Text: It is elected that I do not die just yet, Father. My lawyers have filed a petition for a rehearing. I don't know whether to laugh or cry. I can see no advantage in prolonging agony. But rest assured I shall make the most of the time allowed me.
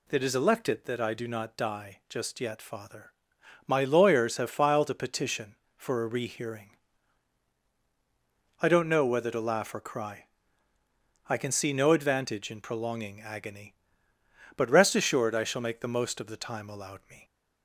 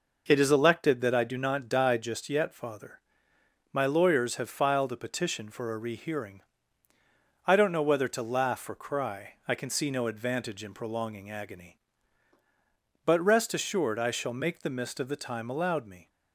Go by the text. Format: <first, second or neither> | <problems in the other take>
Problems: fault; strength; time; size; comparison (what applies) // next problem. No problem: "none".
first | says "mist" for "most"; at 14.6 s